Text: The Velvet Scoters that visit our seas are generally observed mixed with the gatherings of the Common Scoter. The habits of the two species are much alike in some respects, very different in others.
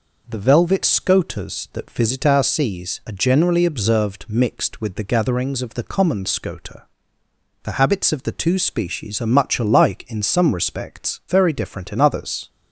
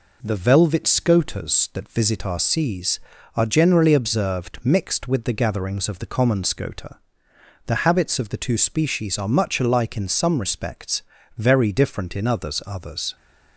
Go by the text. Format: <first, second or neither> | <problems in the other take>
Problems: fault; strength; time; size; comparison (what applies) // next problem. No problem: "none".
first | says "others" twice; at 12.6 s